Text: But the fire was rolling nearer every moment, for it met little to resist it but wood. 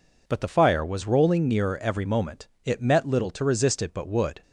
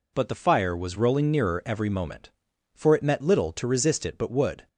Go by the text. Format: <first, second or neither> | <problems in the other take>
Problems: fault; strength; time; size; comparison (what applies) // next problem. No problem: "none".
second | skips "for"; at 2.5 s